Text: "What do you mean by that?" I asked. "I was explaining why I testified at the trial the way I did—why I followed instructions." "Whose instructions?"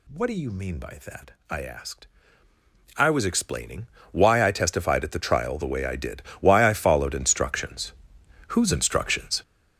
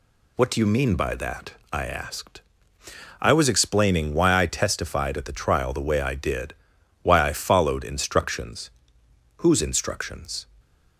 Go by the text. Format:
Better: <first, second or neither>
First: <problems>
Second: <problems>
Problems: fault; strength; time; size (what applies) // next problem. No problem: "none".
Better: second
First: gets louder; strong; throughout; 11.5 dB // pauses between "explaining" and "why"; slight; at 3.8 s; 0.24 s long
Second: none